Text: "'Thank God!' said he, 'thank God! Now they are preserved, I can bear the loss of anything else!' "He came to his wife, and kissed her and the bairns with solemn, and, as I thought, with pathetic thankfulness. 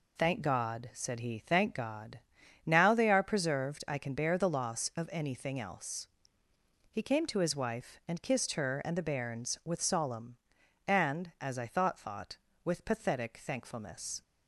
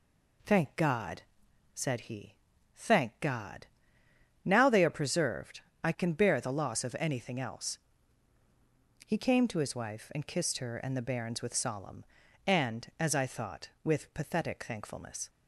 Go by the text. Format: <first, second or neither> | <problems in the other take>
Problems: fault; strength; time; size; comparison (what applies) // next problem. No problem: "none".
second | says "thought" twice; at 11.9 s